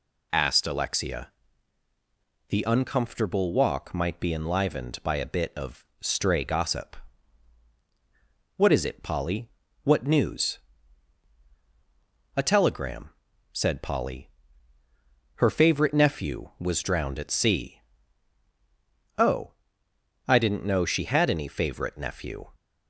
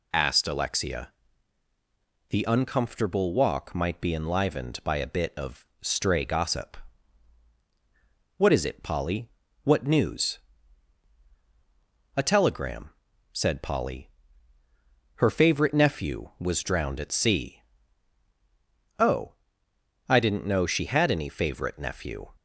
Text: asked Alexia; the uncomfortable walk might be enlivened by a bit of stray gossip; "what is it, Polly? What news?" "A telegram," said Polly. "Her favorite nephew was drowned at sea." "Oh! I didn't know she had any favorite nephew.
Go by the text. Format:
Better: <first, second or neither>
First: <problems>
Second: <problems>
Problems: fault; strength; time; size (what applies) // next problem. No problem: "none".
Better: neither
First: none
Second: none